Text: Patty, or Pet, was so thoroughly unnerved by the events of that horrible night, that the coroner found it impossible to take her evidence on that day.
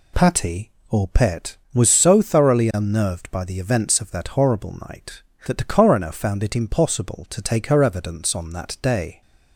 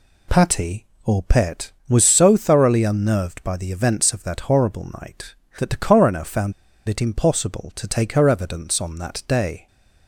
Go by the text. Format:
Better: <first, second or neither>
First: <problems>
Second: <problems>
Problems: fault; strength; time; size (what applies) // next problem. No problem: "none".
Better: first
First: pauses between "horrible" and "night"; slight; at 4.7 s; 0.16 s long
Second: pauses between "horrible" and "night"; slight; at 4.8 s; 0.16 s long // pauses between "found" and "it"; slight; at 6.5 s; 0.36 s long